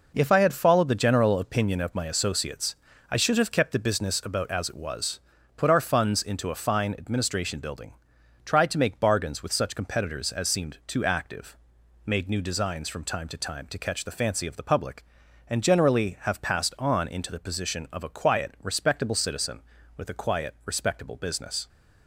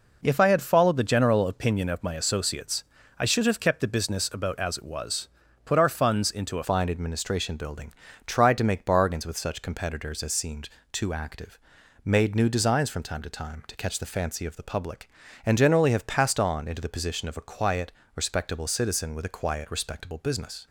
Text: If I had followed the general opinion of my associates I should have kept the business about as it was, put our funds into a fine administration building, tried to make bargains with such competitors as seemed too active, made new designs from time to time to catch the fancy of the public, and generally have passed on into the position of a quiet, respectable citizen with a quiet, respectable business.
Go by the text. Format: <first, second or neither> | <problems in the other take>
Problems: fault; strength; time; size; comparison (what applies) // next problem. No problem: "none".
first | pauses between "associates" and "I"; slight; at 2.8 s; 0.34 s long; slight in the first // changes voice at "fine"; from 6.6 s on; 14.0 s long // pauses between "seemed" and "too"; slight; at 10.6 s; 0.24 s long